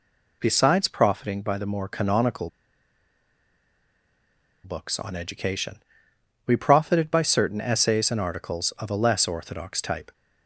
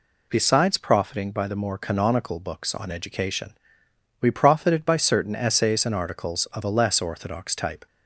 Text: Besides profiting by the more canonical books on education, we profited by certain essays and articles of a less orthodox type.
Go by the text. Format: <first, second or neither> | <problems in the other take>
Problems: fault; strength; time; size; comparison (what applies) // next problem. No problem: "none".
second | pauses between "canonical" and "books"; strong; at 2.4 s; 2.1 s long